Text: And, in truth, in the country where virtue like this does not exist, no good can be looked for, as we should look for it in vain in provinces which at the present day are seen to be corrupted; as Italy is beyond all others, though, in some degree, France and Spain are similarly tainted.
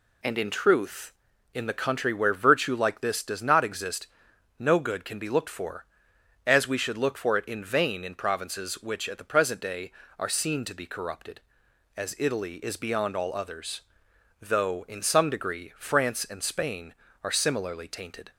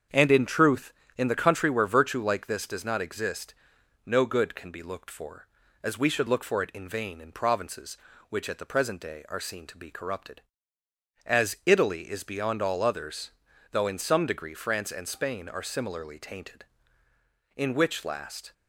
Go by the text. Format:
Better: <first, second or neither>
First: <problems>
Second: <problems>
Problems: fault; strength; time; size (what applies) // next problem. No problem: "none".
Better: first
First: none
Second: starts louder than the rest; strong; until 1.3 s; 7.5 dB // goes on to say "In which last"; noticeable; from 17.5 s on; 0.98 s long